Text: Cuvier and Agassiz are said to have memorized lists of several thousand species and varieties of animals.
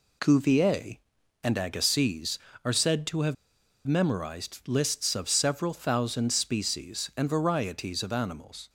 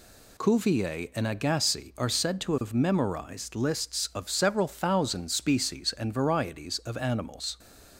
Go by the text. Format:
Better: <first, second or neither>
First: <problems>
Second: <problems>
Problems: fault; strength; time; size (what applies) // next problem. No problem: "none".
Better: second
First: pauses between "have" and "memorized"; noticeable; at 3.3 s; 0.52 s long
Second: none